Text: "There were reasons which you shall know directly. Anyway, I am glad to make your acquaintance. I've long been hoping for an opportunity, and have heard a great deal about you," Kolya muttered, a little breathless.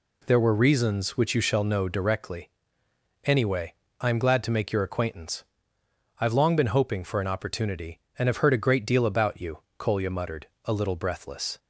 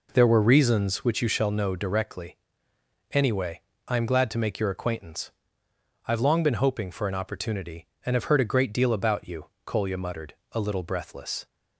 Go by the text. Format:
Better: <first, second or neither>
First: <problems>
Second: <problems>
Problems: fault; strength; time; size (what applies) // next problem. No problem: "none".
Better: first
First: none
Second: starts louder than the rest; noticeable; until 1.1 s; 4 dB